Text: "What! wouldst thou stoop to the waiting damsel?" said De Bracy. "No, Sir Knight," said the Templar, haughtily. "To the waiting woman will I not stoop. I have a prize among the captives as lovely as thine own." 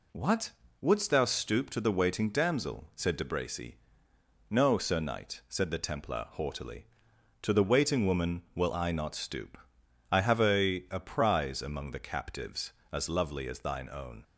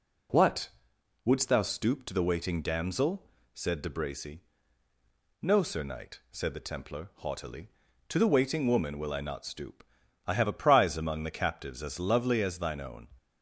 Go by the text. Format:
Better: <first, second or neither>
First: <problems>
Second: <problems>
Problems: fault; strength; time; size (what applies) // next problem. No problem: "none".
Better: second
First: says "a" twice; at 10.9 s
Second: none